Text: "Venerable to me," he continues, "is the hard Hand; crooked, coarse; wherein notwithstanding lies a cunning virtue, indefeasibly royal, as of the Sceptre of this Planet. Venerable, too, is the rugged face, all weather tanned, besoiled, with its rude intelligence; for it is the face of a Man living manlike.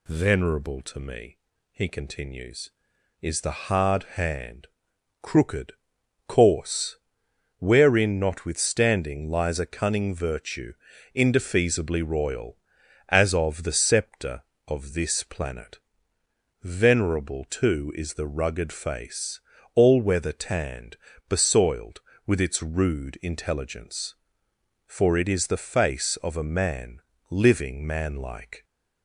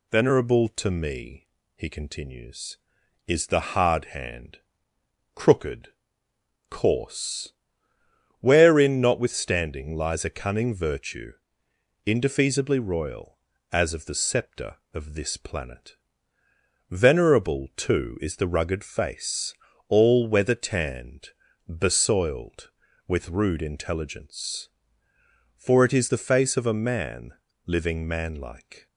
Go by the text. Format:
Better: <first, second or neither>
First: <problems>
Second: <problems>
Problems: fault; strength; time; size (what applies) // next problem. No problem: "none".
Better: first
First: pauses between "Man" and "living"; slight; at 27.0 s; 0.26 s long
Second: skips "its"; at 23.2 s // pauses between "Man" and "living"; slight; at 27.3 s; 0.32 s long